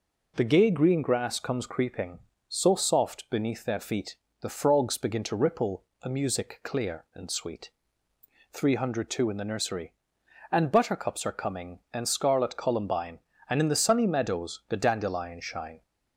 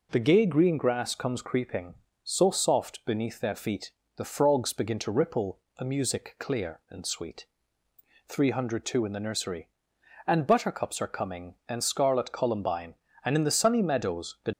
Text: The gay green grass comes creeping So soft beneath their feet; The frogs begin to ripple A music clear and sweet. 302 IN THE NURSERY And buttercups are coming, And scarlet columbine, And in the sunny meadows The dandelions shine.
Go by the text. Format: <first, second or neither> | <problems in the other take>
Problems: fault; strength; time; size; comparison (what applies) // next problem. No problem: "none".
first | pauses between "ripple" and "A"; slight; at 5.5 s; 0.18 s long; slight in the first // stops before "dandelions shine"; at 14.5 s